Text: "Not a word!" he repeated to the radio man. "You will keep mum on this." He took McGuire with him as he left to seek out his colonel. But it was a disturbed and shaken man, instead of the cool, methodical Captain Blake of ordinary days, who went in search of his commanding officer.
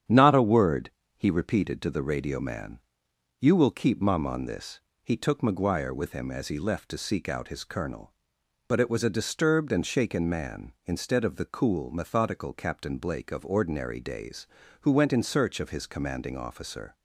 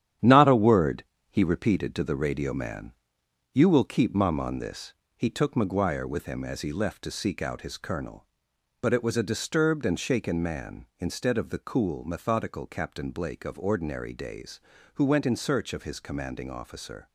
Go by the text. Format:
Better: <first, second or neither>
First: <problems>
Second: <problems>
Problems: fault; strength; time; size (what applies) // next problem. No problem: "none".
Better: first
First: starts louder than the rest; strong; until 1.3 s; 9 dB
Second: gets quieter; strong; throughout; 7.5 dB // starts louder than the rest; strong; until 1.4 s; 10 dB